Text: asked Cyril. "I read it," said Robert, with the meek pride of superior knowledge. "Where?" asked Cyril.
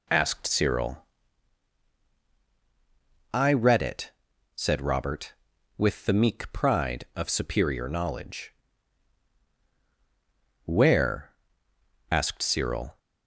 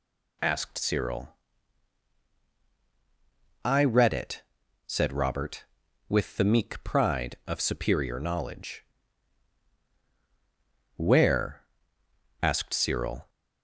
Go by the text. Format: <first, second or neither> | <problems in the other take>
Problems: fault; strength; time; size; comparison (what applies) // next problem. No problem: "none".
second | starts louder than the rest; slight; until 1.4 s; 2 dB